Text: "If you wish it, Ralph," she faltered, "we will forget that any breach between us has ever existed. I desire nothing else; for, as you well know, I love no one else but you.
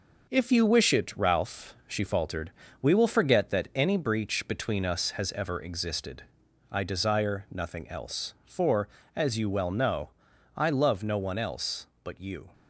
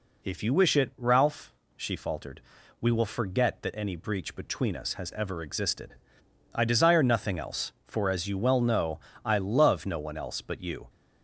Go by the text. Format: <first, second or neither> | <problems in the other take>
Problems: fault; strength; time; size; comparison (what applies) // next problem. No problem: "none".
second | gets quieter; noticeable; throughout; 4.5 dB